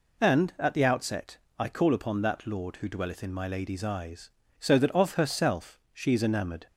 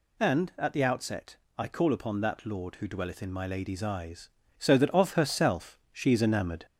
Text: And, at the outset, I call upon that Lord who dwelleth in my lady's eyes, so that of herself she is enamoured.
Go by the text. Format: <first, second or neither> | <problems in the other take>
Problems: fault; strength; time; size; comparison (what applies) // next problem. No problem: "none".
first | gets louder; slight; throughout; 2 dB